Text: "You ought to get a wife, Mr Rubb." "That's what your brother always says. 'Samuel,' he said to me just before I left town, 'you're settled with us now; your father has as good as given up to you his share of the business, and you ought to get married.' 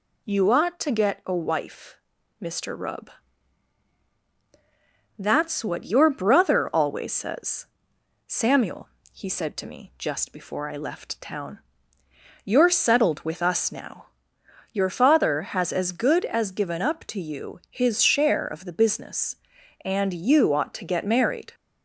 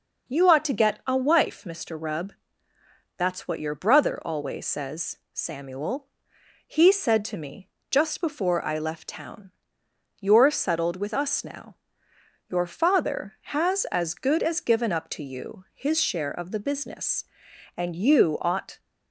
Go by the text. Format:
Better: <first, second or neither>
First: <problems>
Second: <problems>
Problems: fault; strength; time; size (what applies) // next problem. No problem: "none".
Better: first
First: none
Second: pauses between "me" and "just"; slight; at 7.6 s; 0.22 s long // stops before "to get married"; at 18.7 s